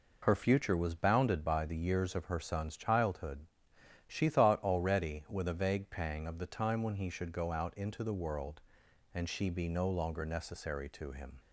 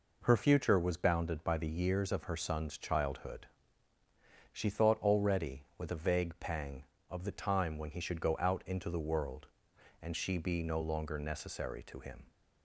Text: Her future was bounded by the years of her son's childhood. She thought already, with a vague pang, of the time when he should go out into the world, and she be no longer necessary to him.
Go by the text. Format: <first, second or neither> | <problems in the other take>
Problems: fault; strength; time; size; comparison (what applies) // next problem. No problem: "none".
neither | none